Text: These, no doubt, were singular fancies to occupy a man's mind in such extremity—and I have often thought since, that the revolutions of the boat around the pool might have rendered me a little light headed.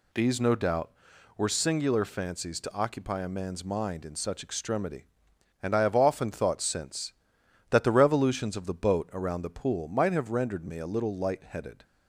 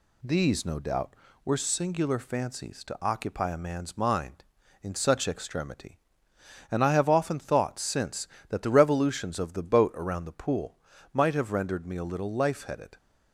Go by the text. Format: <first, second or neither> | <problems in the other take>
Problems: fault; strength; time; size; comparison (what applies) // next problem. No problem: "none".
first | pauses between "pool" and "might"; slight; at 10.7 s; 0.36 s long // says "life" for "light"; at 12.3 s